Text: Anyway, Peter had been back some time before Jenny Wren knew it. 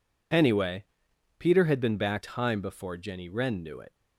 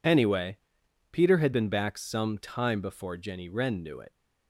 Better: second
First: skips "some"; at 2.2 s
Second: none

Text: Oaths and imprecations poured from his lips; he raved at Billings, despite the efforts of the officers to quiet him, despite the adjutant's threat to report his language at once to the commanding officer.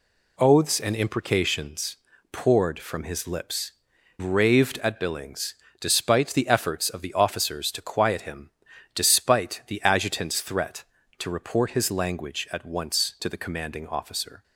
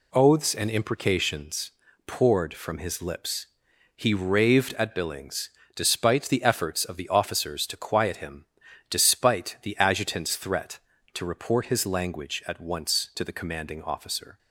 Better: second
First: pauses between "imprecations" and "poured"; slight; at 1.9 s; 0.34 s long // skips "he"; at 3.9 s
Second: pauses between "imprecations" and "poured"; slight; at 1.7 s; 0.34 s long

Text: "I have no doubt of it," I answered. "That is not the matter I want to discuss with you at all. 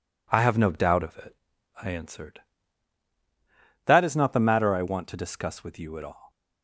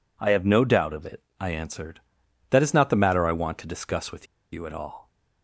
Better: first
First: none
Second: pauses between "with" and "you"; slight; at 4.2 s; 0.26 s long

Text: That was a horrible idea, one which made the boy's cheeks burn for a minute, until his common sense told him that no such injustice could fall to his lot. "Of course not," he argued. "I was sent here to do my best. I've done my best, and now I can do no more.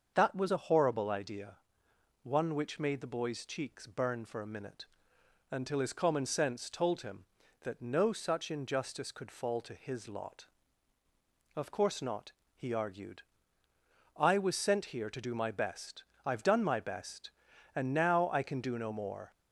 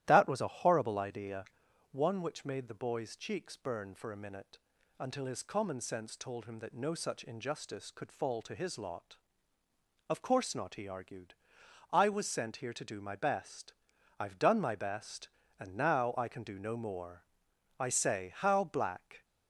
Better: first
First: starts louder than the rest; until 1.1 s; 6.5 dB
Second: starts louder than the rest; strong; until 1.0 s; 13 dB // goes on to say "I say how black"; from 17.7 s on; 1.4 s long

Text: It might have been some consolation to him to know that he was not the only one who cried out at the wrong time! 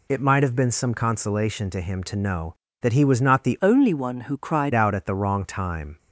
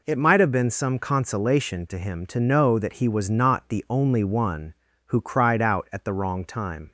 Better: second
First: changes voice from "only" to "cried"; from 3.6 to 4.7 s; 1.1 s long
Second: none

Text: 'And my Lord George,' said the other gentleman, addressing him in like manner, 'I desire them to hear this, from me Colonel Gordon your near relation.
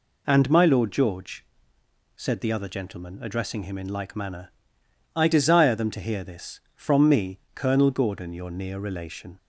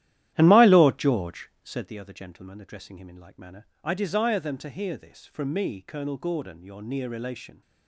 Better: first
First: none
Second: starts louder than the rest; strong; until 1.9 s; 12.5 dB

